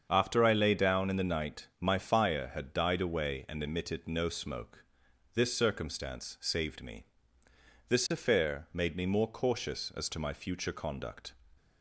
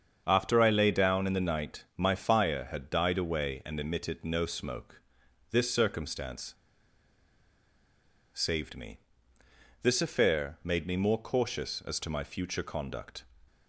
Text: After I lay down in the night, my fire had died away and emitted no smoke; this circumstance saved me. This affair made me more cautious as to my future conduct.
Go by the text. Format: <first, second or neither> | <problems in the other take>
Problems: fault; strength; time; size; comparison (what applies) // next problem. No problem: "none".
first | starts louder than the rest; strong; until 1.2 s; 7 dB; strong in the first // pauses between "circumstance" and "saved"; strong; at 6.5 s; 1.7 s long